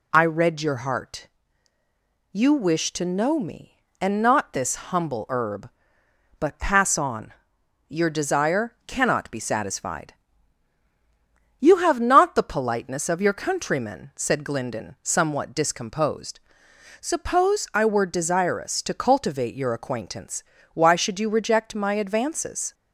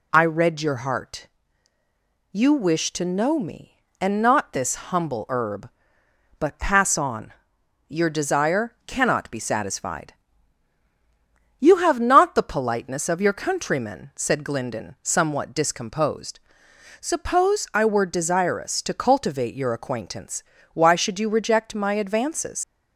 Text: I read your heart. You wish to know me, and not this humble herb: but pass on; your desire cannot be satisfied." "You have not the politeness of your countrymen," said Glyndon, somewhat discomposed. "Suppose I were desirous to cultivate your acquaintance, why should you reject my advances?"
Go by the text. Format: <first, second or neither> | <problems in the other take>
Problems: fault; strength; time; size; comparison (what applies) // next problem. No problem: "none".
first | leaves "advances" unfinished; at 22.6 s; 100 ms